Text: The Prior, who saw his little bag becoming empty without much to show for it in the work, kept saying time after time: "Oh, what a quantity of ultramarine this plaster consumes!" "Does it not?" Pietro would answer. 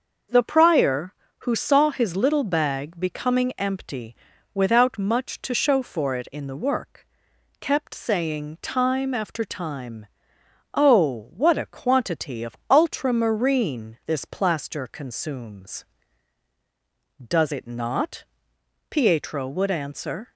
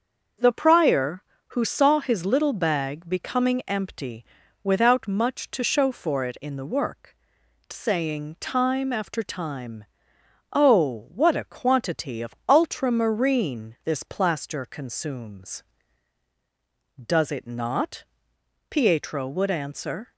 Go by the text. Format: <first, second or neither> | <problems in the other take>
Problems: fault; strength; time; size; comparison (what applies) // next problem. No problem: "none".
first | starts louder than the rest; until 1.6 s; 6.5 dB; noticeable in the first // pauses between "empty" and "without"; at 4.2 s; 0.38 s long; also in the first // skips "kept"; at 7.4 s